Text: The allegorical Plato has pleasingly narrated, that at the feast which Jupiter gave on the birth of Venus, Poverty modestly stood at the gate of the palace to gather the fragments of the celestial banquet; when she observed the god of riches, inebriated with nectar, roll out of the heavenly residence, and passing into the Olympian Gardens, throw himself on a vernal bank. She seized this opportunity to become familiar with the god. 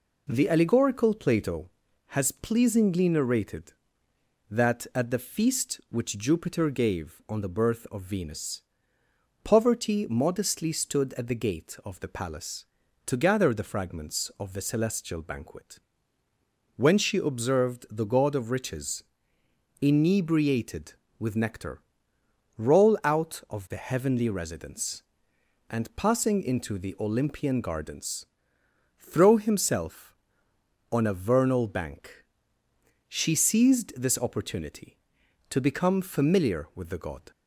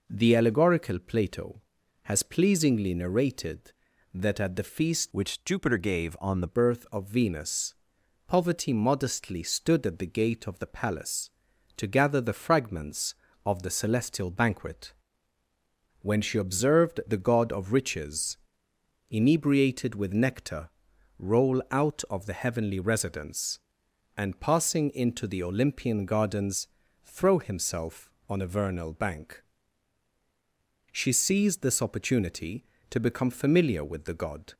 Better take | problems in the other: first | changes voice from "which" to "the"; from 5.1 to 6.4 s; 1.3 s long

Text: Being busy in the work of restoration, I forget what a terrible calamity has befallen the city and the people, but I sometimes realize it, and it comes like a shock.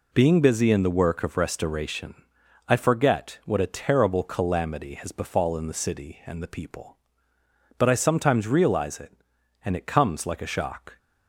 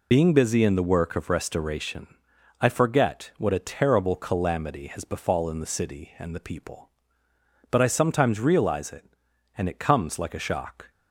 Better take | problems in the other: first | loses the start of "Being"; at 0.1 s; 50 ms

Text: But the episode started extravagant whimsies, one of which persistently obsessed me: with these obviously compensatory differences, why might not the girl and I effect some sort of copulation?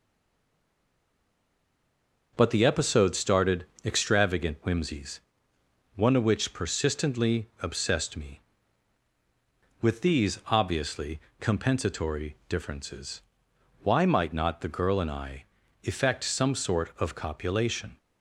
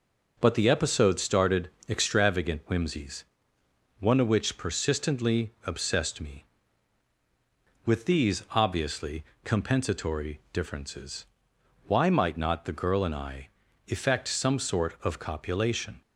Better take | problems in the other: second | stays silent before the first word; until 2.3 s; 2.3 s long // pauses between "started" and "extravagant"; slight; at 3.6 s; 0.20 s long; slight in the second // pauses between "obviously" and "compensatory"; slight; at 11.1 s; 0.20 s long; slight in the second // pauses between "I" and "effect"; at 15.4 s; 0.40 s long; also in the second

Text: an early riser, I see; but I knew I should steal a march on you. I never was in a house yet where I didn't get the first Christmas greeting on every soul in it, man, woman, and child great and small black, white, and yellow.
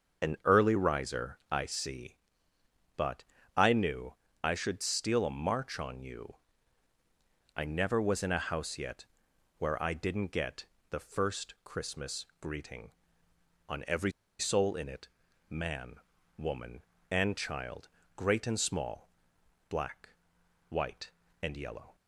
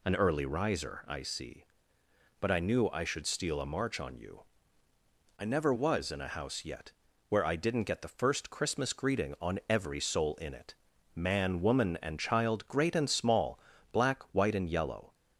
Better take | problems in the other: second | starts louder than the rest; until 1.3 s; 6.5 dB // pauses between "but" and "I"; slight; at 3.2 s; 0.32 s long // pauses between "knew" and "I"; slight; at 4.1 s; 0.30 s long // pauses between "yet" and "where"; noticeable; at 9.0 s; 0.52 s long; also in the second // pauses between "get" and "the"; slight; at 10.6 s; 0.24 s long // pauses between "every" and "soul"; slight; at 14.1 s; 0.27 s long // pauses between "child" and "great"; slight; at 17.8 s; 0.28 s long // pauses between "small" and "black"; noticeable; at 19.0 s; 0.60 s long; slight in the second

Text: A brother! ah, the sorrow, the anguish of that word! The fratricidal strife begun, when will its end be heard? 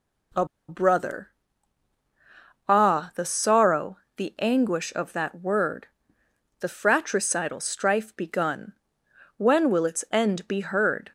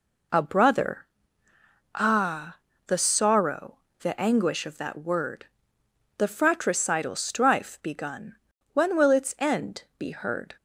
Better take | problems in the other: second | pauses between "A" and "brother"; slight; at 0.4 s; 0.22 s long

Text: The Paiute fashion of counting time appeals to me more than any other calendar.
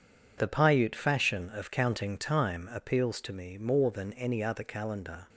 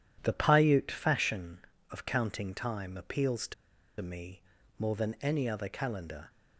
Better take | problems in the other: first | pauses between "to" and "me"; noticeable; at 3.5 s; 0.46 s long // pauses between "me" and "more"; at 4.4 s; 0.38 s long

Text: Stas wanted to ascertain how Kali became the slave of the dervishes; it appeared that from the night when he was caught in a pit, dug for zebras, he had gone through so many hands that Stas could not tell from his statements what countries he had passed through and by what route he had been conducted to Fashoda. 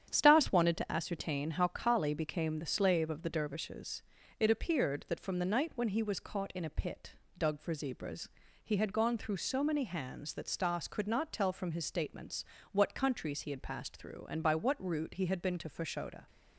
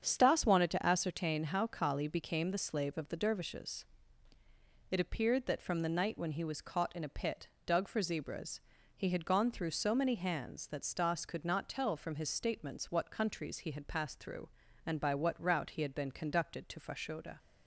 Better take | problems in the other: second | starts louder than the rest; strong; until 1.1 s; 9 dB; strong in the second // pauses between "statements" and "what"; slight; at 12.4 s; 0.28 s long // skips "conducted"; at 15.5 s

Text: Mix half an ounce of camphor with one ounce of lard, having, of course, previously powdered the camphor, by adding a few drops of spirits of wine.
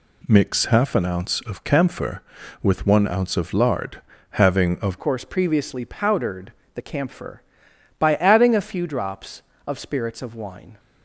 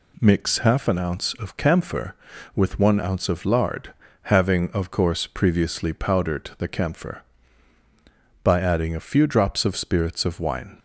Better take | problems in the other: second | changes voice at "course"; from 4.9 s on; 5.8 s long // pauses between "powdered" and "the"; slight; at 6.5 s; 0.22 s long

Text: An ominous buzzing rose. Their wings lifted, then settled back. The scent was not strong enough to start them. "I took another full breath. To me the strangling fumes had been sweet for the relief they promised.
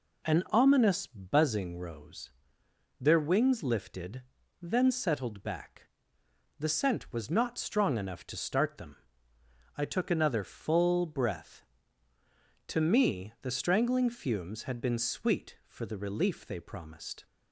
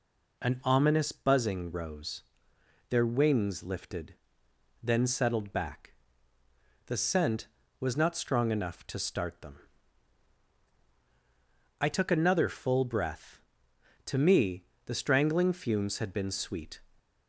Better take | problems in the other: first | pauses between "me" and "the"; slight; at 14.6 s; 0.22 s long // stops before "for the relief they promised"; at 16.9 s

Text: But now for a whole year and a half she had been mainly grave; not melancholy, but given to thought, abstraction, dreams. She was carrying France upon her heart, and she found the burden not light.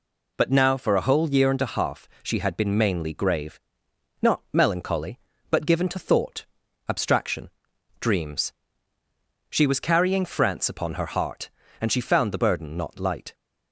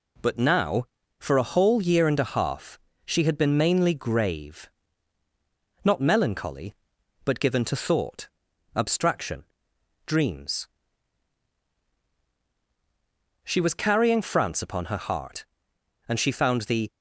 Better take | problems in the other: first | pauses between "half" and "she"; slight; at 2.7 s; 0.26 s long // stops before "burden not light"; at 16.8 s

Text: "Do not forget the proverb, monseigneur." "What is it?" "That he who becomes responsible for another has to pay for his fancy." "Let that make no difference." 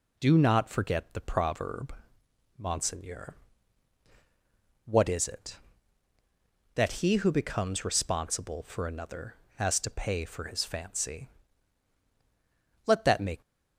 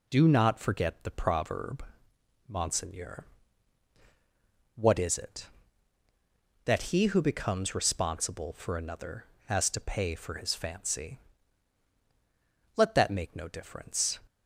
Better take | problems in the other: second | stops before "no difference"; at 13.4 s

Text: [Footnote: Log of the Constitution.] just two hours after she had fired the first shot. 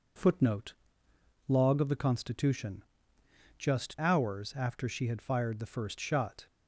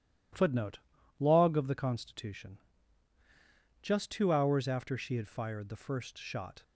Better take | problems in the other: second | skips "two"; at 3.9 s

